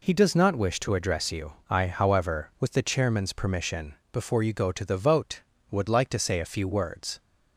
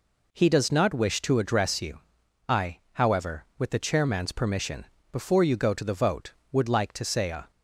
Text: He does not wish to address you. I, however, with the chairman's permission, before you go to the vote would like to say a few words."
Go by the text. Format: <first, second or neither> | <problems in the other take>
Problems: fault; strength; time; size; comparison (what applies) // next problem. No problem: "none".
first | stops before "few words"; at 7.5 s